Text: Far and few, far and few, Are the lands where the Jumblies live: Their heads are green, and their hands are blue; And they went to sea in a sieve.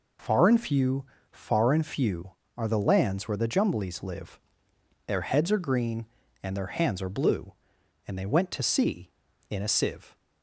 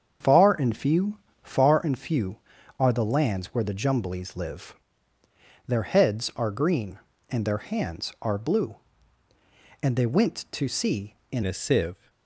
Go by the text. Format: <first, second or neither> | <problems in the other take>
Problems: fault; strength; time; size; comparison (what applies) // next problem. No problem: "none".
first | starts louder than the rest; strong; until 1.4 s; 7.5 dB // changes voice at "a"; from 11.4 s on; 0.6 s long